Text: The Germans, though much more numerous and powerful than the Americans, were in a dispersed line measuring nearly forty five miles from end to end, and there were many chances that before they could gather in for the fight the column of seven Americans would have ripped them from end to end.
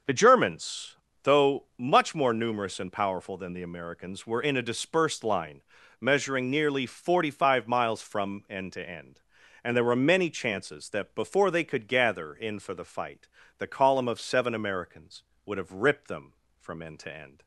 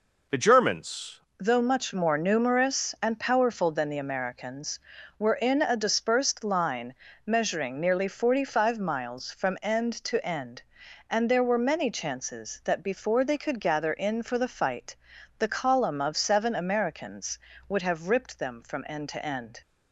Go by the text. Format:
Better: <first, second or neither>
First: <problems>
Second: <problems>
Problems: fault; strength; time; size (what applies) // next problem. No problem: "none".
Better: first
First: pauses between "line" and "measuring"; slight; at 5.6 s; 0.36 s long // pauses between "fight" and "the"; slight; at 13.2 s; 0.32 s long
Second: changes voice at "though"; from 1.3 s on; 18.3 s long // pauses between "line" and "measuring"; slight; at 6.9 s; 0.30 s long // pauses between "fight" and "the"; at 14.9 s; 0.42 s long